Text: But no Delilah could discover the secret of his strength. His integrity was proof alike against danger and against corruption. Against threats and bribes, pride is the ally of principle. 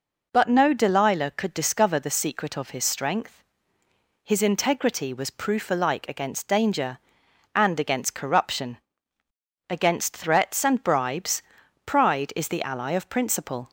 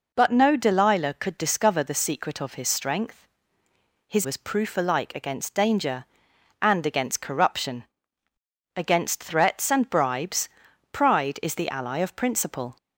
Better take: first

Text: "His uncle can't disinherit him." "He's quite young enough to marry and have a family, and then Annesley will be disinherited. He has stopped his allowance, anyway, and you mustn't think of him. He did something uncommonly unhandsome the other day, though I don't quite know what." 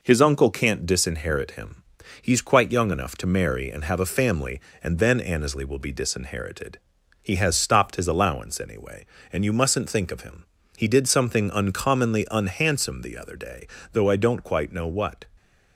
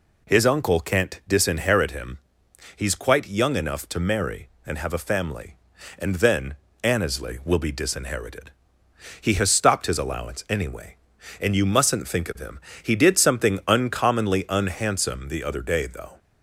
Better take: first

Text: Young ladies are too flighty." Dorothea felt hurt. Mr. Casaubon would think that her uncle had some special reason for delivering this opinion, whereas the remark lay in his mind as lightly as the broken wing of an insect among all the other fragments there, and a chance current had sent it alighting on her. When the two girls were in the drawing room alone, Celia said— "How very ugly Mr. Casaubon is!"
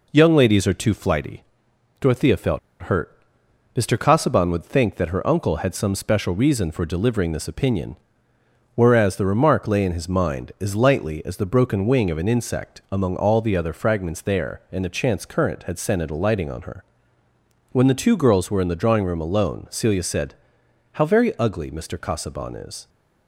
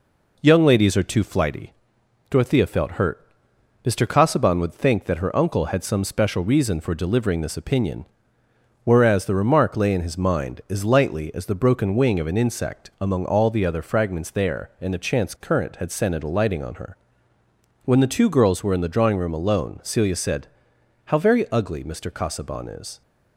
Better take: second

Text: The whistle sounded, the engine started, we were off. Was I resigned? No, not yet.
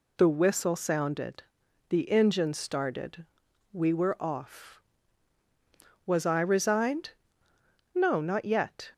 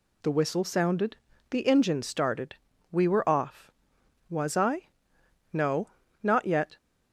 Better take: first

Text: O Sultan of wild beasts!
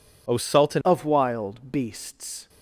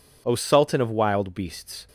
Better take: second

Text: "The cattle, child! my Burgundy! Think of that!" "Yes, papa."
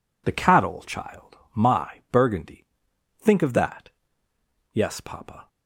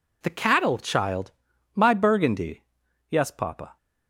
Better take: first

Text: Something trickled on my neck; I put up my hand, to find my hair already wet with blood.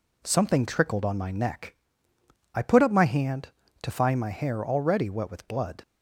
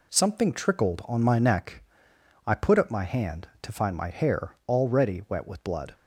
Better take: neither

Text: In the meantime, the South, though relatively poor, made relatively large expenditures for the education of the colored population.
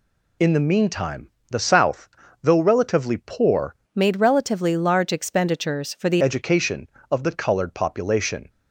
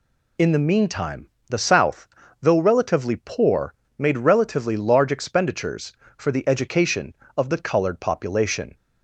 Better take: second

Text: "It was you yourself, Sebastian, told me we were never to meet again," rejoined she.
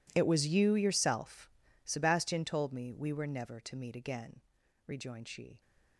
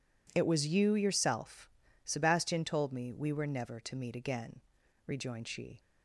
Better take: second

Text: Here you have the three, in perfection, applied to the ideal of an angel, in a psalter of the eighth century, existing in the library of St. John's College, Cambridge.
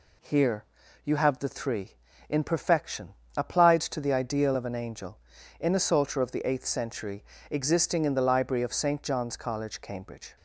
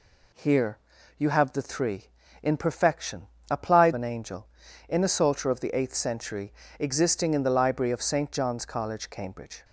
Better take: first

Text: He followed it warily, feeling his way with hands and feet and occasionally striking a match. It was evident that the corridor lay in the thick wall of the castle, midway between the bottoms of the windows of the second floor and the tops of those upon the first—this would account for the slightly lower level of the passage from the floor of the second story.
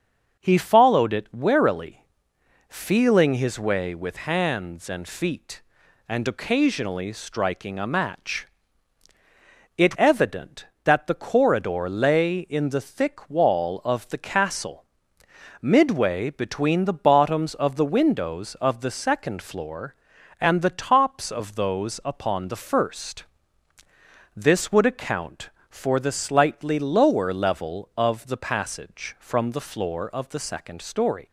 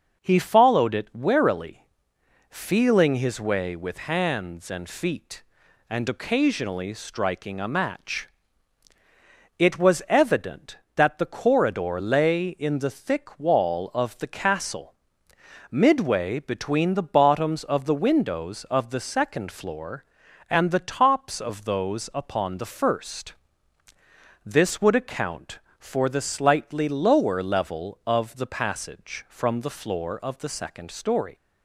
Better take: second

